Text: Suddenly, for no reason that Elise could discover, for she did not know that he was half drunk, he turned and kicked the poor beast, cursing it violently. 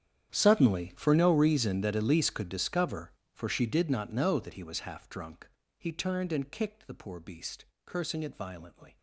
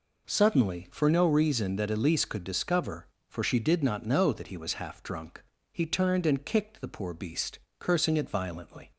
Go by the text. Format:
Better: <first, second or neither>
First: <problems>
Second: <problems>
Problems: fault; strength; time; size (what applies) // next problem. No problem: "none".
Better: second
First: gets quieter; strong; throughout; 19.5 dB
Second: none